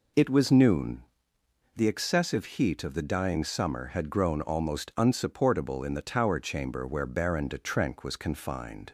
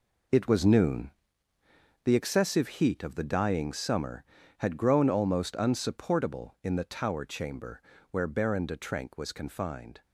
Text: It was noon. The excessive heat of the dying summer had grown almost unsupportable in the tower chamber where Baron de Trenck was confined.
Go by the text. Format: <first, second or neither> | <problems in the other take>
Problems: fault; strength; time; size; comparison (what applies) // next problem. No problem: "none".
first | gets quieter; strong; throughout; 11 dB // pauses between "chamber" and "where"; slight; at 7.8 s; 0.30 s long